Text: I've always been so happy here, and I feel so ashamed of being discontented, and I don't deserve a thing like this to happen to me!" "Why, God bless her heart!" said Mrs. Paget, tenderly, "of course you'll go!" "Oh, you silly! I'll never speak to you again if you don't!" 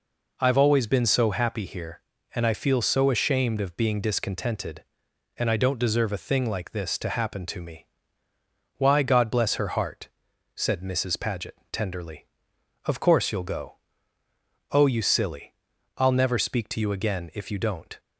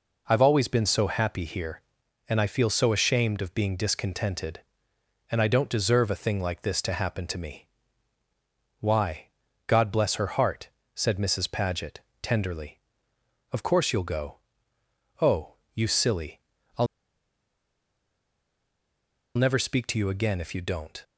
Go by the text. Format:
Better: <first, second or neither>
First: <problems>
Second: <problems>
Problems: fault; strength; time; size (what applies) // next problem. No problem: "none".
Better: first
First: none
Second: pauses between "I'll" and "never"; strong; at 16.8 s; 2.4 s long